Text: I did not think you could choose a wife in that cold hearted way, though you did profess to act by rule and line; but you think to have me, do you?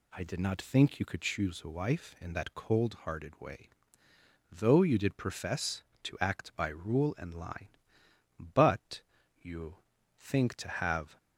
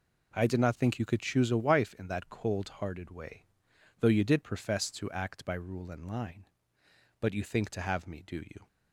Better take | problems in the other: second | pauses between "but" and "you"; at 9.0 s; 0.42 s long // pauses between "you" and "think"; at 9.7 s; 0.40 s long // stops before "me do you"; at 11.1 s

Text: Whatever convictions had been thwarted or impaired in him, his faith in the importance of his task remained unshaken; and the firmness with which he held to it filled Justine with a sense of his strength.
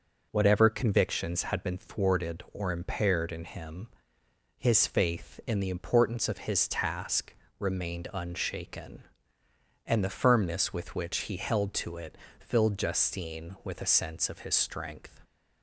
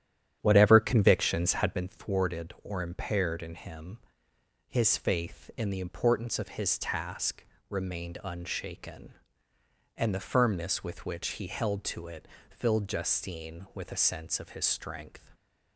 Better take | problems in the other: first | starts louder than the rest; strong; until 1.9 s; 10 dB // pauses between "task" and "remained"; slight; at 7.4 s; 0.26 s long; slight in the first // pauses between "it" and "filled"; slight; at 12.2 s; 0.24 s long; slight in the first

